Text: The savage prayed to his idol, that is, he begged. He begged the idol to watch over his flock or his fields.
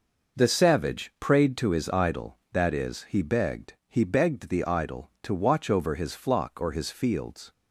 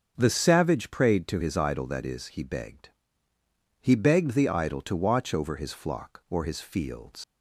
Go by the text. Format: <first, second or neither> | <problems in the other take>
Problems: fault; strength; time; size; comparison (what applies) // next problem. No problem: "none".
first | starts louder than the rest; until 1.1 s; 6.5 dB // leaves "fields" unfinished; at 7.2 s; 95 ms